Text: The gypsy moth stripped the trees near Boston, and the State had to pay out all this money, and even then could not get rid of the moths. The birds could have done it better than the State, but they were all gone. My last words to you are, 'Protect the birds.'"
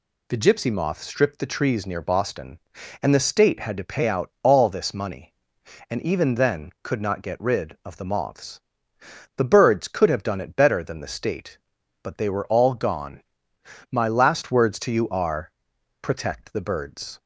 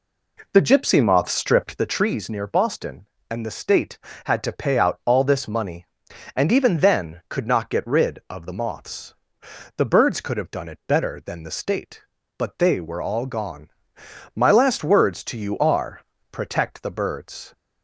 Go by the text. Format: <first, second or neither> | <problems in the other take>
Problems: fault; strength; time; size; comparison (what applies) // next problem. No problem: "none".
first | starts louder than the rest; slight; until 1.9 s; 3 dB